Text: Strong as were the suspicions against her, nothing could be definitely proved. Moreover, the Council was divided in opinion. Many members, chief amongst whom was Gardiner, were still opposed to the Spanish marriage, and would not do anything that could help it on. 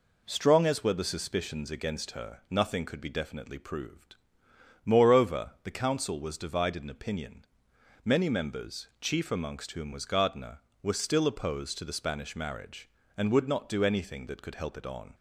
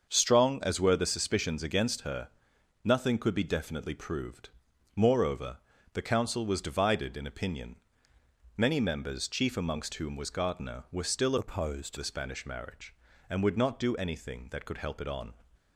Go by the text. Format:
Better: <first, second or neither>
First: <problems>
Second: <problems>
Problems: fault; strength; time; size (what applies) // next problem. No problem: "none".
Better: first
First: none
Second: starts louder than the rest; until 1.1 s; 7 dB // changes voice from "opposed" to "to"; from 11.3 to 11.9 s; 0.6 s long